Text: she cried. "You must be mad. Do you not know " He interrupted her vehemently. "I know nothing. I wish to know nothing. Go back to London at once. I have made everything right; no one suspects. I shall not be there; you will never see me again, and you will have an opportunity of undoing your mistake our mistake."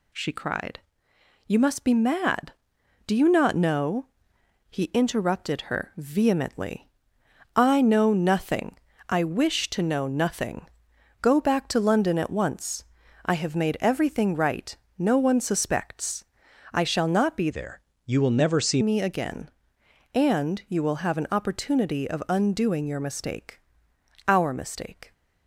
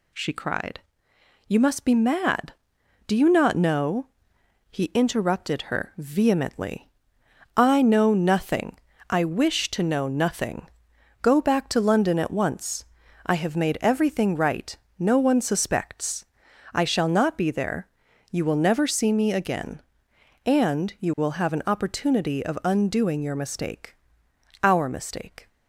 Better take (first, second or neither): second